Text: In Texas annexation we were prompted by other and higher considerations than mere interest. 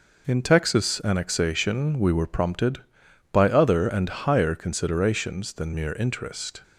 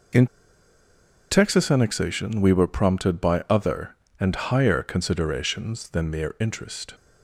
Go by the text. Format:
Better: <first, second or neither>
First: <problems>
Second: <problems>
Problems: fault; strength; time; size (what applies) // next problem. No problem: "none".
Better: first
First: none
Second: pauses between "In" and "Texas"; at 0.2 s; 1.0 s long